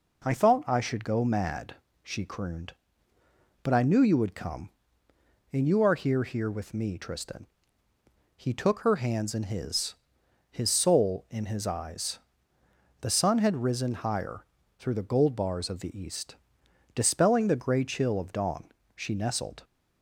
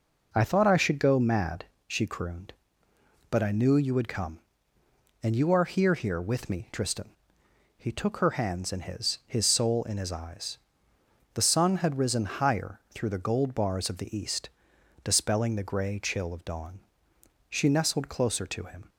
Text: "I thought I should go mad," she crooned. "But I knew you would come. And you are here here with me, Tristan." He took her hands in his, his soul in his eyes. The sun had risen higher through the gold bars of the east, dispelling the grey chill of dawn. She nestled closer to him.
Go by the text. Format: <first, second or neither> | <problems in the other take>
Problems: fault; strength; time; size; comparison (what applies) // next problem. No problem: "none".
second | pauses between "higher" and "through"; slight; at 14.4 s; 0.34 s long // stops before "closer to him"; at 19.6 s